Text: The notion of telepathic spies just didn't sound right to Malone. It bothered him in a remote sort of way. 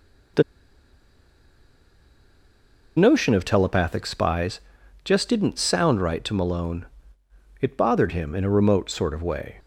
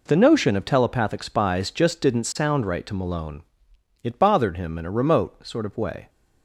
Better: second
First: pauses between "The" and "notion"; strong; at 0.4 s; 2.5 s long // pauses between "spies" and "just"; at 4.6 s; 0.42 s long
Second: none

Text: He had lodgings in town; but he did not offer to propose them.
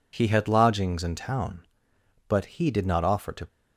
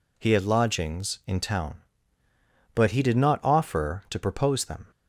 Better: second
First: stops before "propose them"; at 3.4 s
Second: none

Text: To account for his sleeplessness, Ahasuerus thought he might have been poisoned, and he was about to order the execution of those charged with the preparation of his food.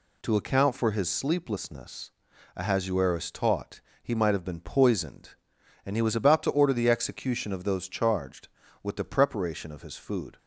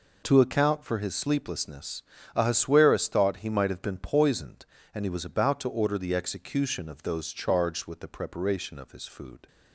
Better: second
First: says "taught" for "thought"; at 3.3 s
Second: none

